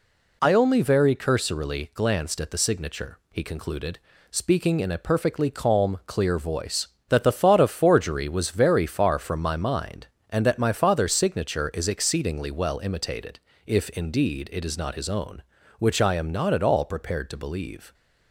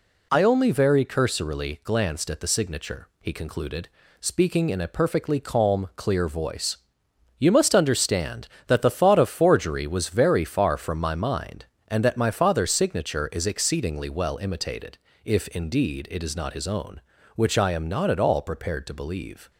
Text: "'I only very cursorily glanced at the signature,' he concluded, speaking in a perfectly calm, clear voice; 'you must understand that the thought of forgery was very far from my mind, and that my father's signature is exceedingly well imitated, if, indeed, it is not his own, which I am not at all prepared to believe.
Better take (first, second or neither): second